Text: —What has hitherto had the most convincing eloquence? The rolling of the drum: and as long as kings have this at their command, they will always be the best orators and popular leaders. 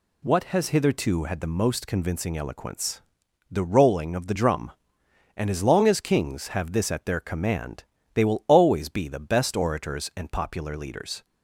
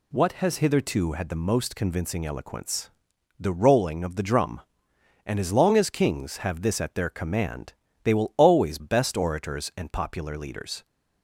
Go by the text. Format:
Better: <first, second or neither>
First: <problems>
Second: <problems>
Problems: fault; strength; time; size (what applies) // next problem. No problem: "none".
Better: first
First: none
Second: skips "be the"; at 8.7 s